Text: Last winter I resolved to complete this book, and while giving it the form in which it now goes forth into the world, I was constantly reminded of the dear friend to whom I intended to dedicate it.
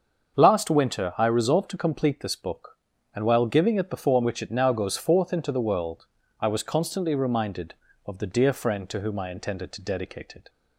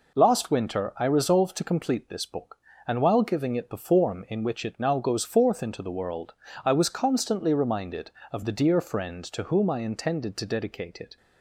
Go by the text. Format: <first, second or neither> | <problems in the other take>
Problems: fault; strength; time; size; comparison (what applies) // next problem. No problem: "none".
second | starts louder than the rest; until 1.4 s; 7 dB // skips "in"; at 4.2 s